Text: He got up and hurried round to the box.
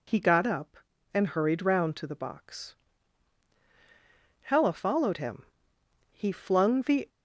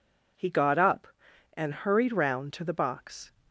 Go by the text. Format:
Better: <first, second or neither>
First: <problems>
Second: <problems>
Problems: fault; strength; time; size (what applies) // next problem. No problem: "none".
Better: second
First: goes on to say "Hella followed him He flung the"; strong; from 4.4 s on; 2.6 s long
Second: none